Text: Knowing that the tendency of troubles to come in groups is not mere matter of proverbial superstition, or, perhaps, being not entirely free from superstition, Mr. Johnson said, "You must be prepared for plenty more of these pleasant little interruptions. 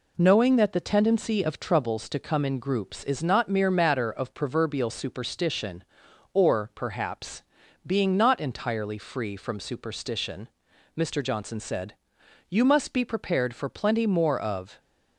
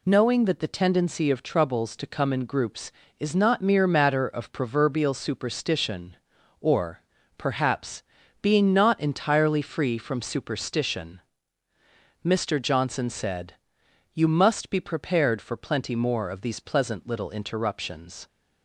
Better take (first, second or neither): second